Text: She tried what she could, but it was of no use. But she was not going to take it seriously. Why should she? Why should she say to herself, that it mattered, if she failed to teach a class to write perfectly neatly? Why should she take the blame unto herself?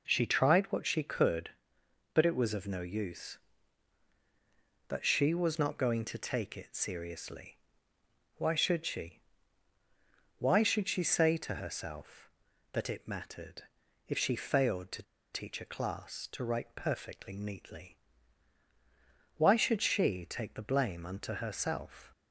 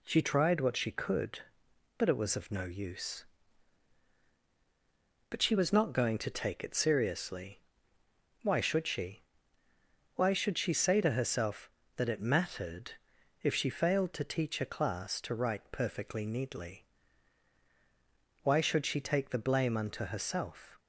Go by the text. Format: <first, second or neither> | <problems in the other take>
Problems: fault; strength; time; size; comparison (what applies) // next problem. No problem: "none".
second | pauses between "to" and "teach"; slight; at 15.0 s; 0.30 s long